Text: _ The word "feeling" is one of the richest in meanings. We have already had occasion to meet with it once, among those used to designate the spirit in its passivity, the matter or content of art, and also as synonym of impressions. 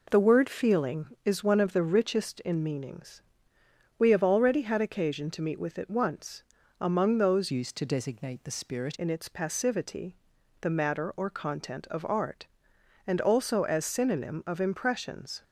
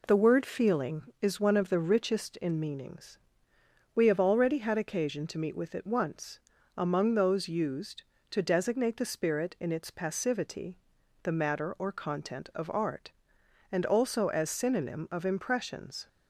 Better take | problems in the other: second | changes voice from "used" to "spirit"; from 7.5 to 8.9 s; 1.4 s long

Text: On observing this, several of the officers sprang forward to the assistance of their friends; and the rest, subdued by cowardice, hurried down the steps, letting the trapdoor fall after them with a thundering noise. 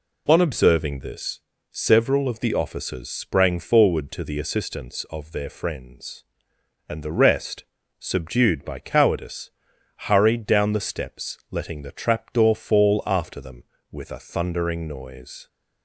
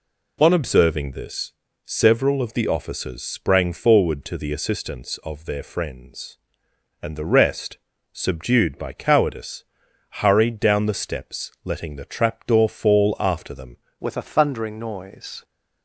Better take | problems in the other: first | changes voice at "with"; from 14.0 s on; 1.4 s long

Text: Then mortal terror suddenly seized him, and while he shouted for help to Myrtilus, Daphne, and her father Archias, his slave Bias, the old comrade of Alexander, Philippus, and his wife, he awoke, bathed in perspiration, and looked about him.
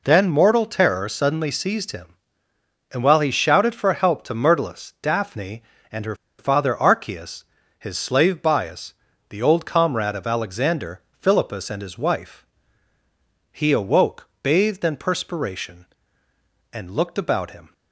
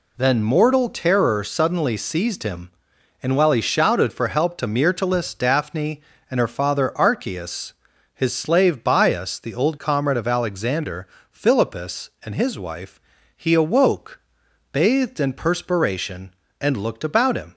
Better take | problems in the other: second | pauses between "her" and "father"; slight; at 6.1 s; 0.24 s long

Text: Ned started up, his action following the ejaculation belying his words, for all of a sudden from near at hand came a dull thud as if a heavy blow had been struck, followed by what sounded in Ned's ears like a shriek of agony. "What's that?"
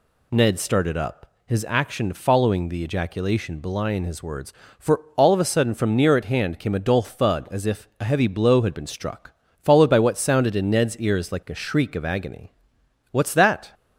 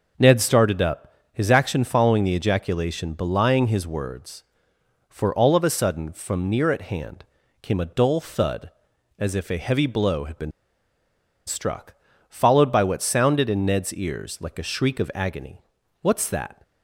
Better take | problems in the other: first | pauses between "hand" and "came"; slight; at 7.2 s; 0.36 s long // pauses between "been" and "struck"; noticeable; at 10.5 s; 0.96 s long

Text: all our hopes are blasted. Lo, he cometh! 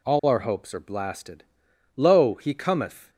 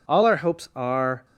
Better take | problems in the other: first | stops before "blasted Lo he cometh"; at 1.2 s

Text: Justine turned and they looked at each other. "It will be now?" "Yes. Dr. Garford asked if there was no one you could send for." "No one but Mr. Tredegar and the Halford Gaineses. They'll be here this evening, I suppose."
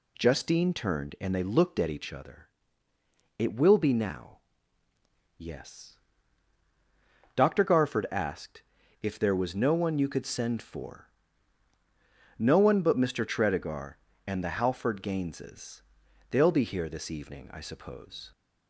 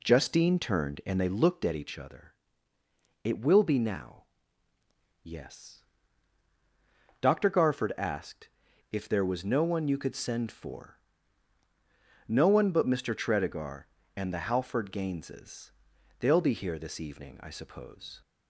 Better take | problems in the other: first | starts louder than the rest; slight; until 1.5 s; 2 dB // pauses between "asked" and "if"; at 8.4 s; 0.43 s long; also in the first

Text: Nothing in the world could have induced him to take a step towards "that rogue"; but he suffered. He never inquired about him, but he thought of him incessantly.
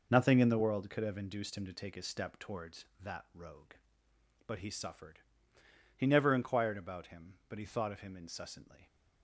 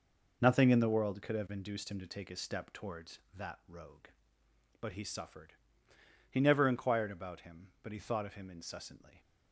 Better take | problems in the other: neither | none

